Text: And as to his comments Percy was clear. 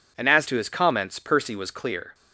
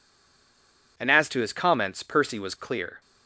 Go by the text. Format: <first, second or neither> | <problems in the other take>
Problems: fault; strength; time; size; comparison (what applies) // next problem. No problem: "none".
first | stays silent before the first word; until 0.9 s; 0.9 s long